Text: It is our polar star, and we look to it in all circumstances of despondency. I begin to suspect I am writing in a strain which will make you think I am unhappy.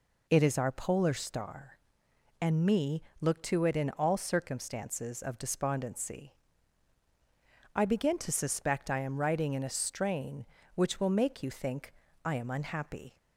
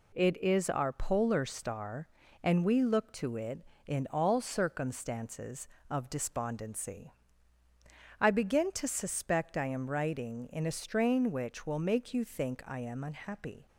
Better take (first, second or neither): second